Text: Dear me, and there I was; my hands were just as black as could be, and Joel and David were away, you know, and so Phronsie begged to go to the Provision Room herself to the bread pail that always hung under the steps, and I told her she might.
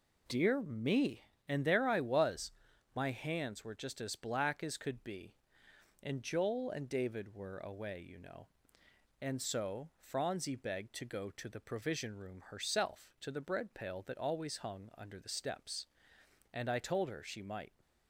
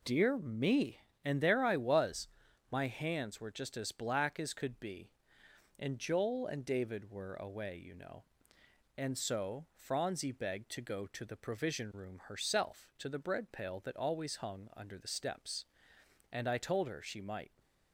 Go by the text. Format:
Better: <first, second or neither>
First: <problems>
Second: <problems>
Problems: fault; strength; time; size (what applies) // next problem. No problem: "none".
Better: neither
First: none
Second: none